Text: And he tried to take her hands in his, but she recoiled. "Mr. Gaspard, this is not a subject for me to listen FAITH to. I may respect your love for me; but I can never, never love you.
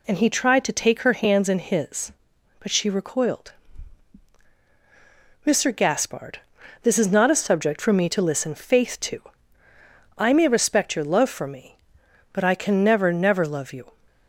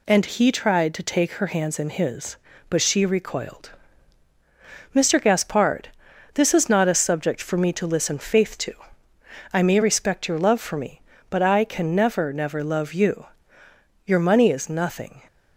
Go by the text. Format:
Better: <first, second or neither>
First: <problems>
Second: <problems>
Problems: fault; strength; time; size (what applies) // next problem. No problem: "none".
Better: first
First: none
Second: goes on to say "Your money is nothing"; noticeable; from 14.0 s on; 1.1 s long